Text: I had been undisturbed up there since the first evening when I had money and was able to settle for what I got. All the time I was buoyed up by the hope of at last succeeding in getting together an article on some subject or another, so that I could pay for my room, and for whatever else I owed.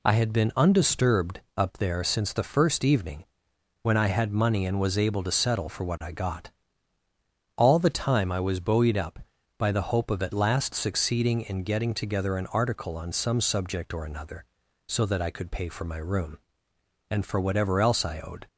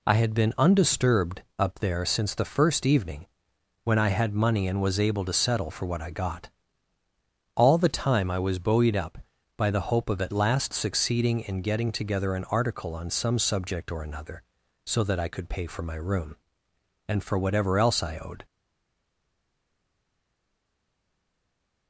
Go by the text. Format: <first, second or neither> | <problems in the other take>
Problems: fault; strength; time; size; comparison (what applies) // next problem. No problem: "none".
first | pauses between "undisturbed" and "up"; slight; at 1.4 s; 0.18 s long; slight in the first // pauses between "evening" and "when"; noticeable; at 3.2 s; 0.58 s long; noticeable in the first // stays silent after the last word; strong; from 18.4 s on; 3.4 s long